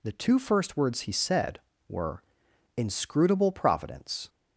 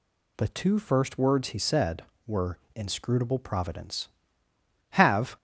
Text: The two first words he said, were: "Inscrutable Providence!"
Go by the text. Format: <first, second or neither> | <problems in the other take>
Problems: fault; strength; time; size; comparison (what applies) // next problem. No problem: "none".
first | goes on to say "Have"; slight; from 4.9 s on; 0.44 s long